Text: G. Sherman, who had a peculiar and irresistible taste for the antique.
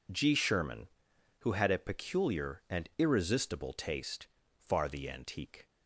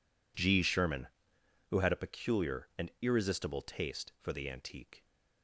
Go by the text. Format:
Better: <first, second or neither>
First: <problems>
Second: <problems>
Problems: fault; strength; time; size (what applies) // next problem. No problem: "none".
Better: second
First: says "far" for "for"; at 4.5 s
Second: none